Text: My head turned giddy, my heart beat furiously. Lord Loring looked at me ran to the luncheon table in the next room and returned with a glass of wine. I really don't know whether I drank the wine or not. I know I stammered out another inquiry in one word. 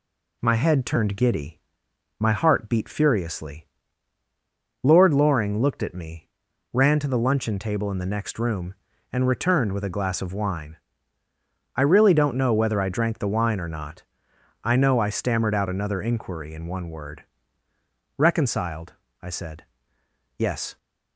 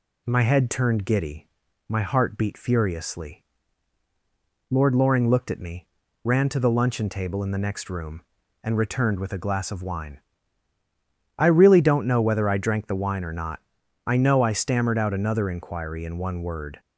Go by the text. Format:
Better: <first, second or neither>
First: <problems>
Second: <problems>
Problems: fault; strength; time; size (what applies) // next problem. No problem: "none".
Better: second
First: pauses between "me" and "ran"; noticeable; at 6.2 s; 0.48 s long // goes on to say "Reconciled I said Yes"; strong; from 18.1 s on; 2.5 s long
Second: pauses between "me" and "ran"; slight; at 5.8 s; 0.36 s long